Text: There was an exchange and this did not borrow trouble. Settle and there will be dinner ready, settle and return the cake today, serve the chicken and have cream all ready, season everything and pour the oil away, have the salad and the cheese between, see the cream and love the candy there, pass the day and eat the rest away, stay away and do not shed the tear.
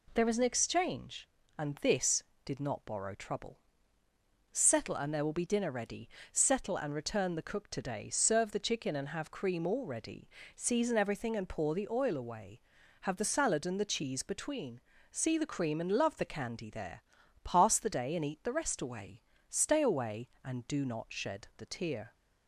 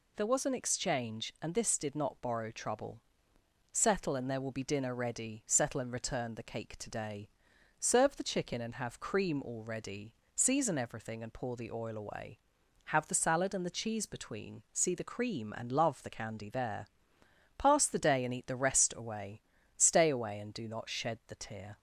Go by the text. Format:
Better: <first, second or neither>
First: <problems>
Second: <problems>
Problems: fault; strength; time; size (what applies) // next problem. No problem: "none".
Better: second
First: says "cook" for "cake"; at 7.4 s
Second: none